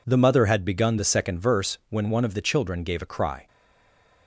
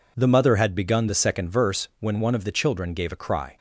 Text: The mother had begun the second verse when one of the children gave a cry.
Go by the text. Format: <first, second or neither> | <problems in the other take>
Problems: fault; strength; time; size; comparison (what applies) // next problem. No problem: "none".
second | stays silent after the last word; slight; from 3.4 s on; 0.8 s long